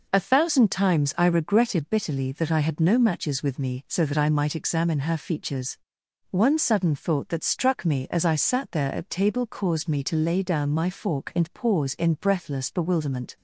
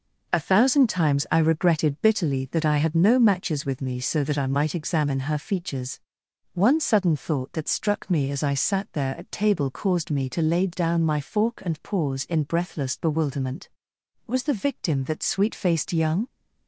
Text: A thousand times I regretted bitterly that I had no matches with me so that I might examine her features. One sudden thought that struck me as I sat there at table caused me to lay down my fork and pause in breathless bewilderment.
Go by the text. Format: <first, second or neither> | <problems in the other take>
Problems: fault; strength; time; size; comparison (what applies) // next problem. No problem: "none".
first | goes on to say "Was the victim that sweet faced young"; strong; from 14.2 s on; 2.0 s long